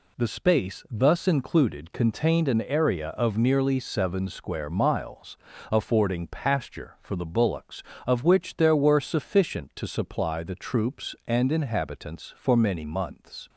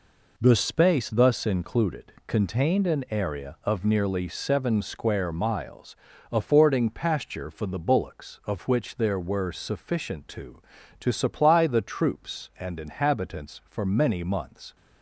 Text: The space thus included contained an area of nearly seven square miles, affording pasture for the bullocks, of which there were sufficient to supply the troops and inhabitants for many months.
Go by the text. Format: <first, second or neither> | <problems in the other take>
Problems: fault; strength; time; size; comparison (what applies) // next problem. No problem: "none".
first | says "to" twice; at 11.0 s